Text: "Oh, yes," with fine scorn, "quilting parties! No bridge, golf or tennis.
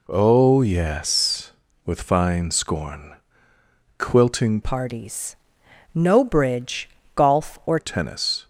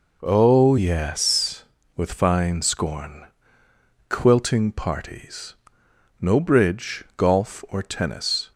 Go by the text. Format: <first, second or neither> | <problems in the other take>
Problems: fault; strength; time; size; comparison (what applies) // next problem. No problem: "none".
second | changes voice from "parties" to "or"; from 4.6 to 7.7 s; 3.1 s long